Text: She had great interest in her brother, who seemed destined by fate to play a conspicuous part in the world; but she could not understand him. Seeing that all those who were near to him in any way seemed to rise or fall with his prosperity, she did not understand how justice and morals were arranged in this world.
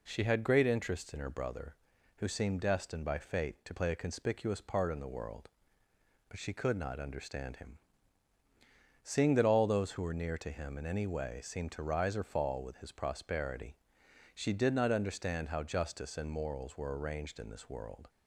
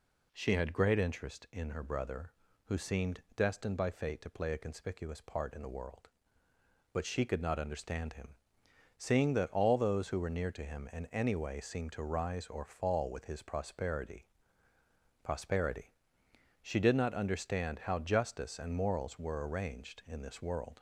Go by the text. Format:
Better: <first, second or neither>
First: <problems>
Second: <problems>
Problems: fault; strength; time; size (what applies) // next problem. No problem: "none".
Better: first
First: none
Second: says "prosperity" twice; at 15.2 s